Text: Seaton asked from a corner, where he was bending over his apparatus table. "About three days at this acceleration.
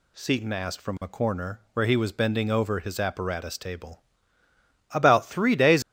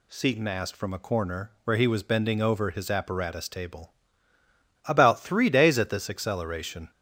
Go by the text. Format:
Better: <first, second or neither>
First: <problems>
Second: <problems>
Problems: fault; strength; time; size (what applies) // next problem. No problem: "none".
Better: second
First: stops before "at this acceleration"; at 5.8 s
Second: none